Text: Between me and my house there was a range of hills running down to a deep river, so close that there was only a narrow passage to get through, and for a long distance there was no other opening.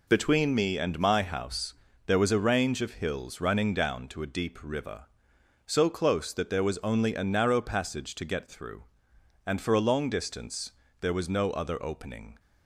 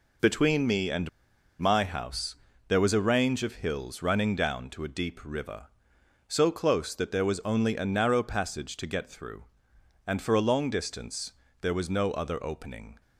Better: first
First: pauses between "house" and "there"; slight; at 1.7 s; 0.32 s long // pauses between "distance" and "there"; slight; at 10.7 s; 0.28 s long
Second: pauses between "and" and "my"; noticeable; at 1.0 s; 0.50 s long // pauses between "house" and "there"; slight; at 2.3 s; 0.32 s long // pauses between "distance" and "there"; slight; at 11.3 s; 0.28 s long

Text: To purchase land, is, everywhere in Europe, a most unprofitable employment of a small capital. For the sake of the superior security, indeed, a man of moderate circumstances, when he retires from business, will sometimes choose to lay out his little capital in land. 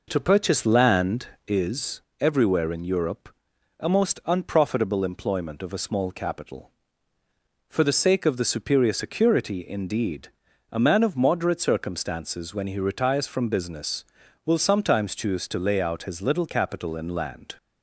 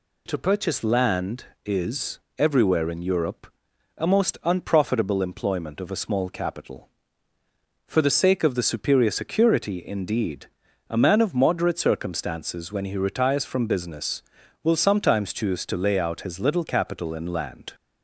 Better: second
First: starts louder than the rest; noticeable; until 1.7 s; 5 dB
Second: none

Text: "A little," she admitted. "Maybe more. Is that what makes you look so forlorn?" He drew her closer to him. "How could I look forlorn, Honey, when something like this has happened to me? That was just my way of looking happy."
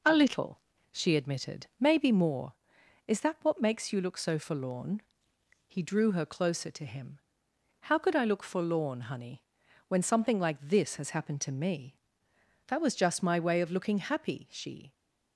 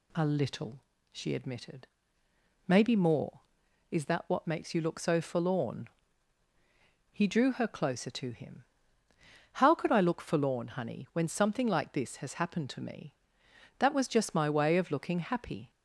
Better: second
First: goes on to say "She"; slight; from 14.4 s on; 0.44 s long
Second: none

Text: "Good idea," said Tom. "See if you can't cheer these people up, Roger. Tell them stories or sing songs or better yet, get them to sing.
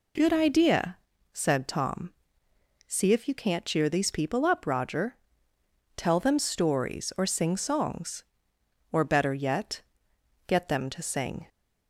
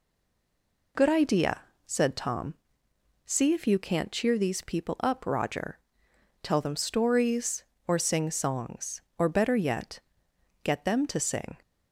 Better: first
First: none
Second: stays silent before the first word; slight; until 0.9 s; 0.9 s long

